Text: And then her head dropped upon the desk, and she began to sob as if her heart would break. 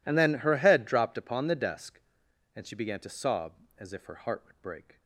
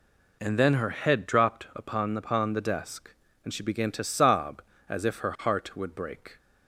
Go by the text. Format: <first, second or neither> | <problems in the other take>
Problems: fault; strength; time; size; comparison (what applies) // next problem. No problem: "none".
first | says "upon" twice; at 2.1 s